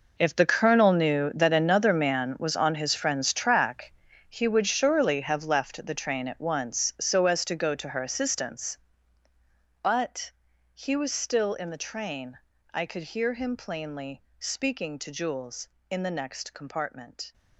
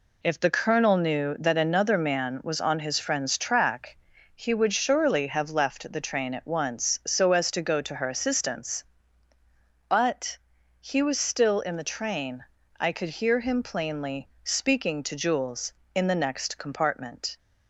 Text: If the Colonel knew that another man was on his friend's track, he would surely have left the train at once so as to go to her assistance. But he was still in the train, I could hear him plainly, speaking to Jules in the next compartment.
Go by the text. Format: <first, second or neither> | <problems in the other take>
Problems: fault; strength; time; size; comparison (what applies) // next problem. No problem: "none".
second | gets quieter; strong; throughout; 14.5 dB // pauses between "But" and "he"; at 10.3 s; 0.42 s long; also in the second